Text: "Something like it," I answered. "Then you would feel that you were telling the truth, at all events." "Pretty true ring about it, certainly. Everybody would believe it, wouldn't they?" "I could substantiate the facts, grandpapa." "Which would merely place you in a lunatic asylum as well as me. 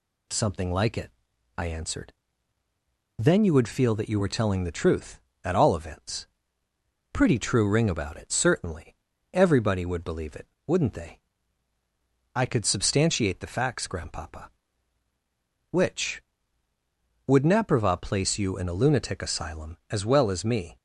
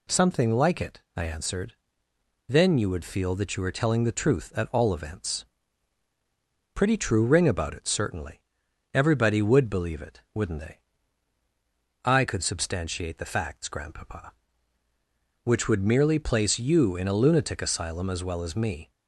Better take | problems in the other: second | says "naprava" for "merely"; at 17.4 s

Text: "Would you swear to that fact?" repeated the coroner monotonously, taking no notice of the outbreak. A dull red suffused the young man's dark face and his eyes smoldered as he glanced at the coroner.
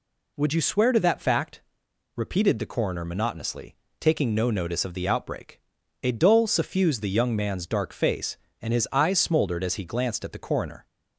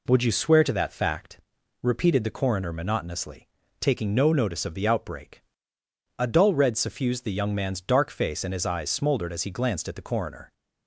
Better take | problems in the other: second | skips "red"; at 6.4 s

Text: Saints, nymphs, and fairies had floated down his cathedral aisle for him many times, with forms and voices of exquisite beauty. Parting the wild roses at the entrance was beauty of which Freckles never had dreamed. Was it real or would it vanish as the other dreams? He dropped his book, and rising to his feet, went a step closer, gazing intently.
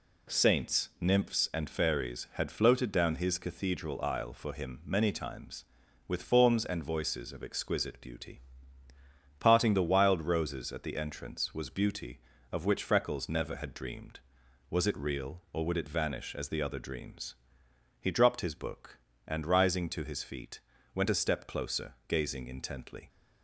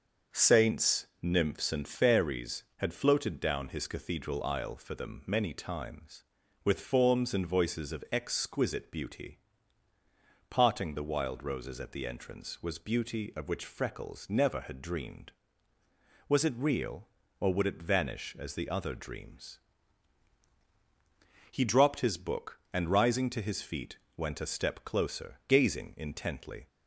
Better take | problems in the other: first | starts louder than the rest; until 1.4 s; 6.5 dB // says "them" for "him"; at 4.9 s

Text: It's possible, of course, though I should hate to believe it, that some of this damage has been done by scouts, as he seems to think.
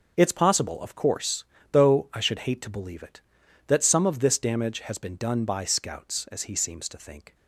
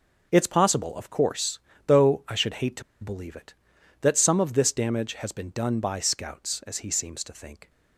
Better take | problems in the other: first | starts louder than the rest; until 1.3 s; 6 dB; noticeable in the first // pauses between "to" and "believe"; slight; at 2.8 s; 0.18 s long

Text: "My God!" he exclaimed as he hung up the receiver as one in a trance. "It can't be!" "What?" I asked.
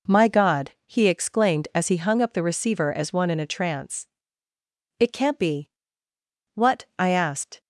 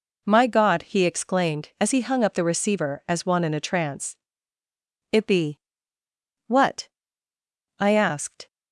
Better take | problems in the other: first | skips "can't"; at 5.2 s

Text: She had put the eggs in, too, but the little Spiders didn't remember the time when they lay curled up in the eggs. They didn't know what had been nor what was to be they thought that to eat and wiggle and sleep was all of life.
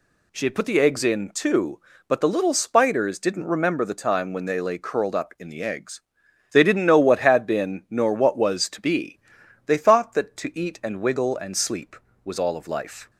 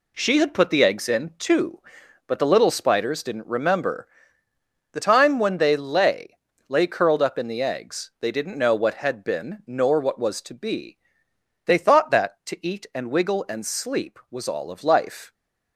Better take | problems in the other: first | pauses between "remember" and "the"; noticeable; at 4.0 s; 0.86 s long // says "lay" twice; at 6.6 s // pauses between "be" and "they"; noticeable; at 10.9 s; 0.68 s long; noticeable in the first

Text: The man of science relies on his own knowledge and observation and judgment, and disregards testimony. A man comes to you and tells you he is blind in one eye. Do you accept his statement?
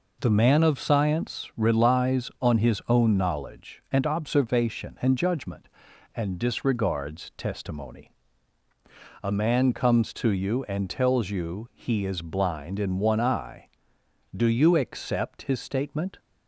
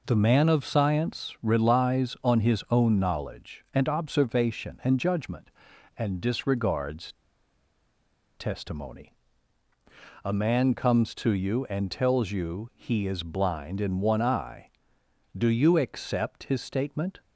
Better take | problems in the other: first | pauses between "disregards" and "testimony"; at 7.1 s; 1.2 s long

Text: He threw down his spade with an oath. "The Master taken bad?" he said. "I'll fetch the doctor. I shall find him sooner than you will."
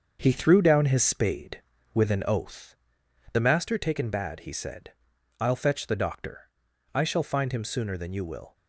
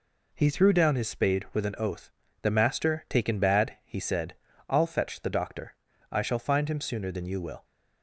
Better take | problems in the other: second | gets quieter; throughout; 7 dB

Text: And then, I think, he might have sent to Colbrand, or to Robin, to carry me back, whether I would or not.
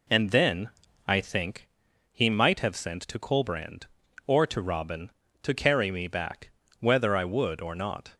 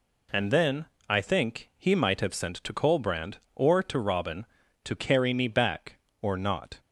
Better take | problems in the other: first | skips "whether I would"; at 6.0 s

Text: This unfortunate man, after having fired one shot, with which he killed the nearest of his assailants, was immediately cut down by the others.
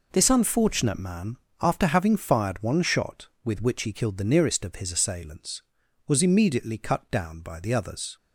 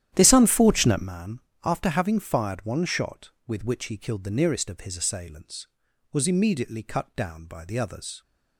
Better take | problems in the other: first | starts louder than the rest; strong; until 1.1 s; 11.5 dB

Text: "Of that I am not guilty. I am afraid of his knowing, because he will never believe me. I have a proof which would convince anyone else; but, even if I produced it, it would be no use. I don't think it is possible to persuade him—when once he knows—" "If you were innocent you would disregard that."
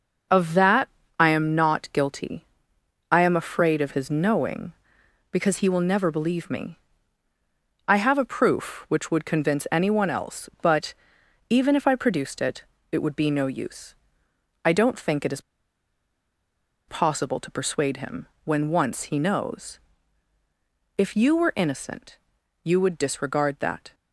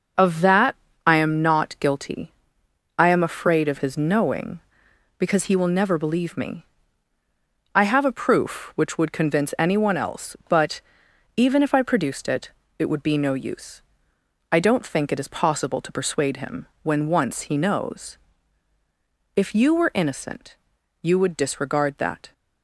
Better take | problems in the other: second | starts louder than the rest; noticeable; until 1.6 s; 6 dB; noticeable in the second // pauses between "that" and "I"; slight; at 0.8 s; 0.30 s long; slight in the second // pauses between "is" and "possible"; strong; at 15.4 s; 1.4 s long // pauses between "innocent" and "you"; at 22.1 s; 0.44 s long; also in the second

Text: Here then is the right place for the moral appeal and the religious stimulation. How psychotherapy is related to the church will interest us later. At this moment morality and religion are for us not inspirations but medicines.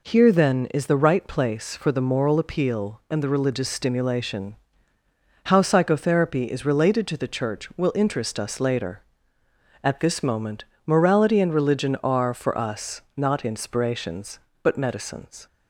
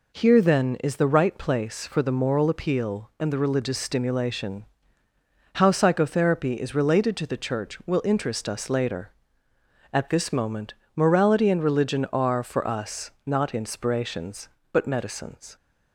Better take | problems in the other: neither | pauses between "moment" and "morality"; slight; the same in both

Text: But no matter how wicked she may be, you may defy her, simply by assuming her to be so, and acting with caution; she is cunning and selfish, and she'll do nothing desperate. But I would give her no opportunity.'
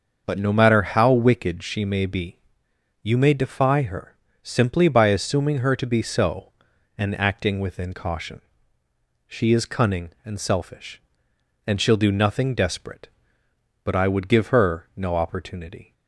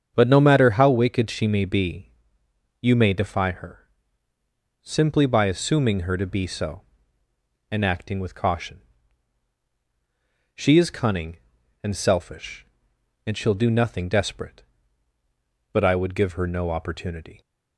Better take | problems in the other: second | starts louder than the rest; until 1.2 s; 6 dB; strong in the second // says "within" for "with"; at 7.5 s

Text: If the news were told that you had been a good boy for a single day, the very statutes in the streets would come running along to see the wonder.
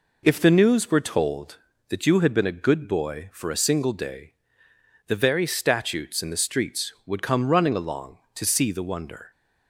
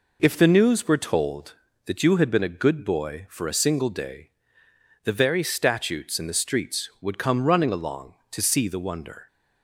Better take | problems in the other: neither | none

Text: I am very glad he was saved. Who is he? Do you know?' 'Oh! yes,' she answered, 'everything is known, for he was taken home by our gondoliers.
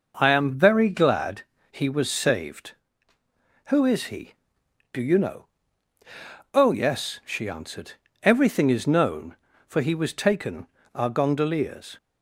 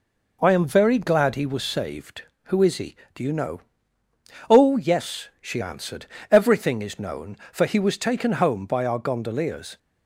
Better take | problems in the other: second | pauses between "glad" and "he"; slight; at 1.4 s; 0.30 s long // skips "home by"; at 10.8 s

